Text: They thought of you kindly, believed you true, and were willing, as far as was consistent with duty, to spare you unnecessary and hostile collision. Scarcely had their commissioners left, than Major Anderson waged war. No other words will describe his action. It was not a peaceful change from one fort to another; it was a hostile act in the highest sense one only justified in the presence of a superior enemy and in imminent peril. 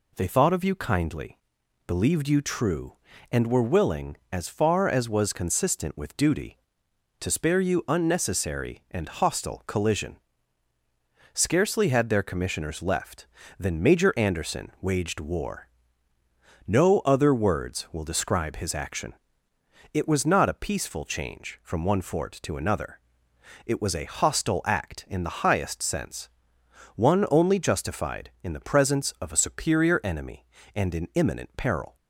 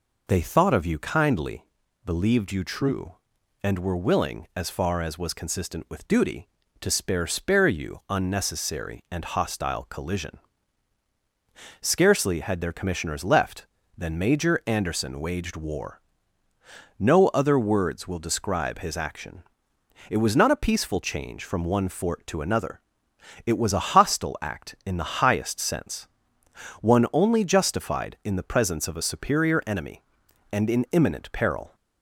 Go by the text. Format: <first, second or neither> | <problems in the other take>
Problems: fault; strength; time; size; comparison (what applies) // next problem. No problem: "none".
first | says "spare" twice; at 7.2 s // pauses between "sense" and "one"; noticeable; at 26.0 s; 0.72 s long; noticeable in the first